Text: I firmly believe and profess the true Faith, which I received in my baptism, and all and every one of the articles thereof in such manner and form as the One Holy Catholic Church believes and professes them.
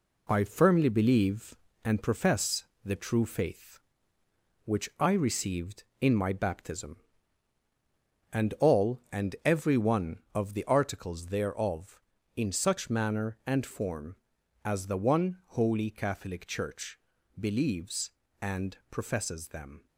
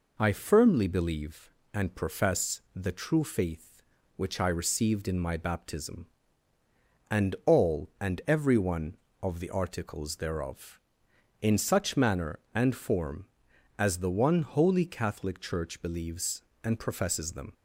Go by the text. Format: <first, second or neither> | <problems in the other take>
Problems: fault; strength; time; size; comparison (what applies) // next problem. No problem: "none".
second | gets quieter; noticeable; throughout; 6 dB // pauses between "profess" and "the"; slight; at 2.6 s; 0.18 s long // pauses between "Church" and "believes"; at 16.9 s; 0.40 s long